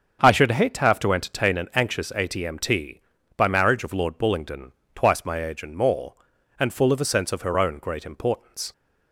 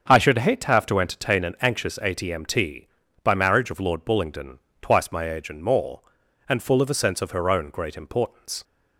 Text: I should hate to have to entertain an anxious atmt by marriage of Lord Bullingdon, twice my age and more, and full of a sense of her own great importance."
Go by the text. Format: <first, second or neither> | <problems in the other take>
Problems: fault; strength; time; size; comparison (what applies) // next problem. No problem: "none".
neither | starts louder than the rest; the same in both